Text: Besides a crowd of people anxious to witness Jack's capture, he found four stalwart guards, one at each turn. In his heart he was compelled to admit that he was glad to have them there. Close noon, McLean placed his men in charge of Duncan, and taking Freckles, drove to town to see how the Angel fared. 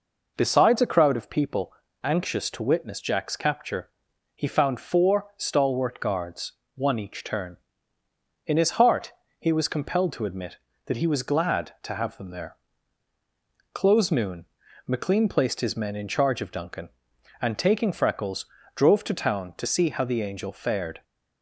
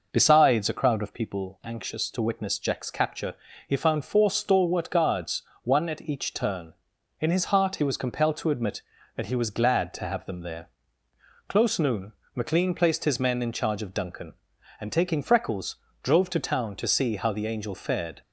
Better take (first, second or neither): second